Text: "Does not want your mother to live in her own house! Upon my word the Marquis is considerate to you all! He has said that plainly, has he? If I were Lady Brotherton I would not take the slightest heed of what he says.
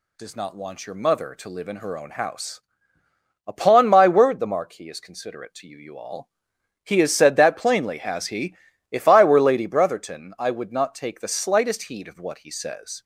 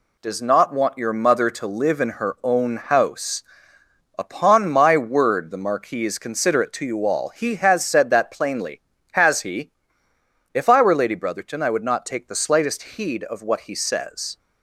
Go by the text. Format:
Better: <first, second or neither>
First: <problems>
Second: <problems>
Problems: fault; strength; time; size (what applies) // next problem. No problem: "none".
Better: second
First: says "you" twice; at 5.7 s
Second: none